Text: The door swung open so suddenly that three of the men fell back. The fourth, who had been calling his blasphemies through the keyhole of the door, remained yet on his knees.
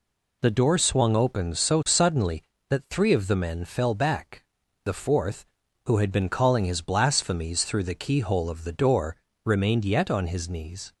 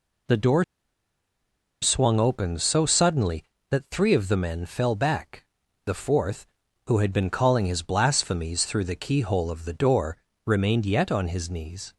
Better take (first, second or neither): first